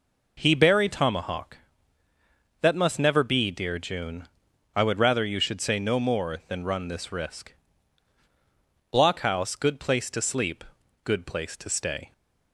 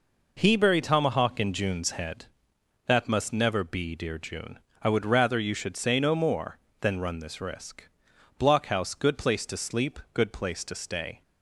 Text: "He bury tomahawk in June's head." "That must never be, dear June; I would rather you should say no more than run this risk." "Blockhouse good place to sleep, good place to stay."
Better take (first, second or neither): second